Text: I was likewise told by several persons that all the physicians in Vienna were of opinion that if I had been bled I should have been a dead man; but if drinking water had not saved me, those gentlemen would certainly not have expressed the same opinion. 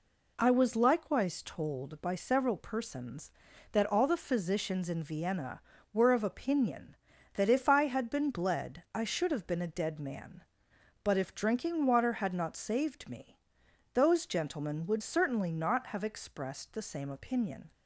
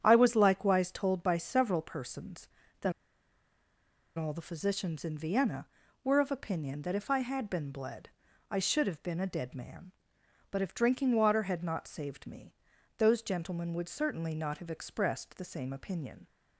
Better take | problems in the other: first | starts louder than the rest; strong; until 1.0 s; 8.5 dB // pauses between "that" and "all"; strong; at 2.9 s; 1.2 s long // pauses between "bled" and "I"; at 8.0 s; 0.40 s long

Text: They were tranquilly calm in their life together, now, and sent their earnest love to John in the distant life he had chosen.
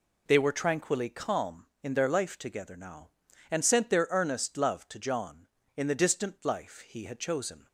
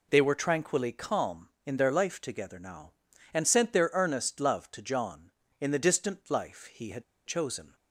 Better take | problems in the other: first | pauses between "had" and "chosen"; slight; at 7.0 s; 0.22 s long

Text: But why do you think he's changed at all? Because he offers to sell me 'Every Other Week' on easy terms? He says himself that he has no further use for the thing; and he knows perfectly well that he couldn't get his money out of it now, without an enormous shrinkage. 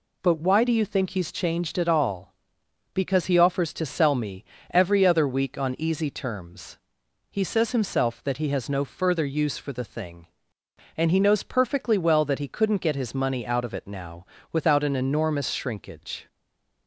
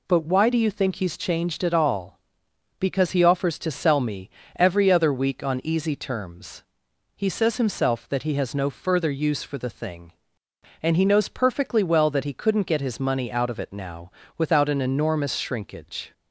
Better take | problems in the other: second | pauses between "me" and "Every"; slight; at 4.4 s; 0.24 s long; slight in the second // stays silent after the last word; slight; from 16.2 s on; 0.6 s long

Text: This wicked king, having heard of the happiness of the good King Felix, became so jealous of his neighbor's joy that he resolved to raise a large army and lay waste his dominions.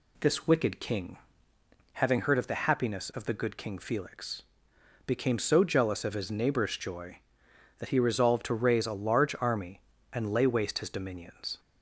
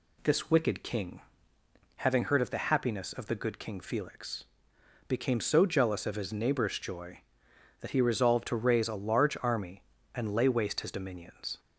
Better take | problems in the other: neither | none

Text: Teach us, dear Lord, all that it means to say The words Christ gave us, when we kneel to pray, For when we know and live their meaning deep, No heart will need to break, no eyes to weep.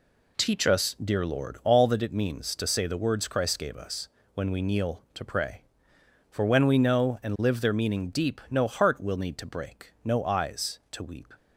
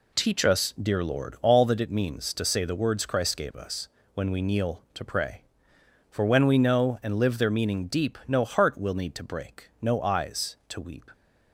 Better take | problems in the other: neither | none

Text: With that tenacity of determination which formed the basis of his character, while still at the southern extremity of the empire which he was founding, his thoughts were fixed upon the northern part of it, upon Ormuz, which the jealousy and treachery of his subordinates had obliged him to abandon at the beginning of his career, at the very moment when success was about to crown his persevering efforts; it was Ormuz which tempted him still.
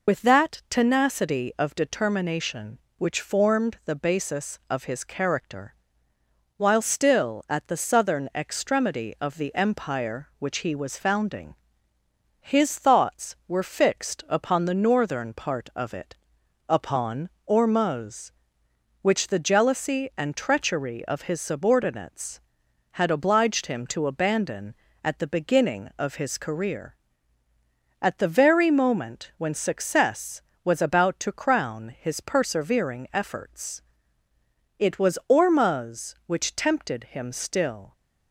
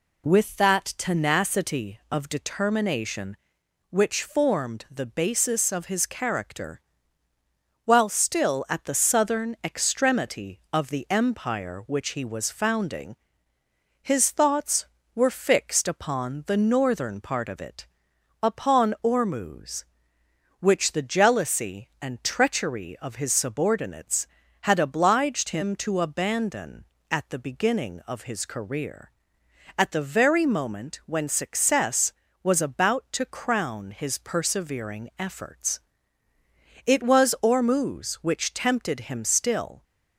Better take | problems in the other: second | loses the start of "With"; at 0.0 s; 50 ms // pauses between "upon" and "Ormuz"; slight; at 17.2 s; 0.18 s long

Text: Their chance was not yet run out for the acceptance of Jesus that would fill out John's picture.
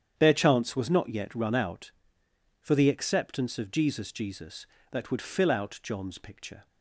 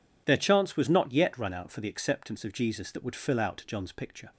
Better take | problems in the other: second | starts louder than the rest; strong; until 1.1 s; 9 dB // says "Jesus" twice; at 4.1 s

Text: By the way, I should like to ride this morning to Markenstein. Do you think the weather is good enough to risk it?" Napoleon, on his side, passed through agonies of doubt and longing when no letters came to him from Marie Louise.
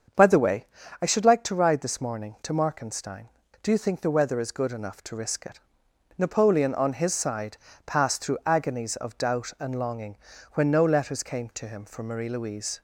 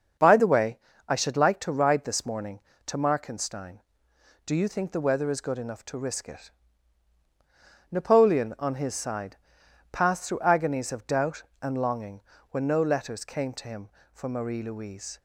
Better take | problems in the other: neither | starts louder than the rest; the same in both // pauses between "longing" and "when"; slight; the same in both

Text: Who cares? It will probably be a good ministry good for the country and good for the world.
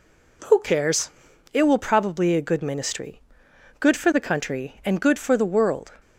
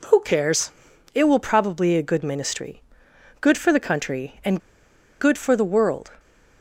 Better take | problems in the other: first | pauses between "ministry" and "good"; noticeable; at 2.8 s; 0.62 s long; noticeable in the first // pauses between "and" and "good"; noticeable; at 4.6 s; 0.59 s long

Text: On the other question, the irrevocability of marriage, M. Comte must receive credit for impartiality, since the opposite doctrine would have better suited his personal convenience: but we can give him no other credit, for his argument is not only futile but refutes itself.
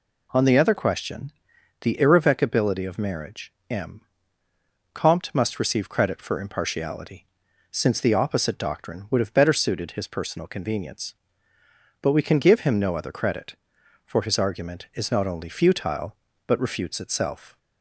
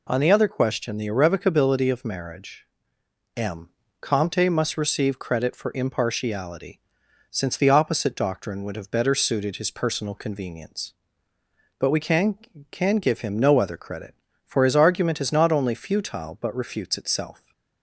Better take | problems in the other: first | says "can" twice; at 12.7 s

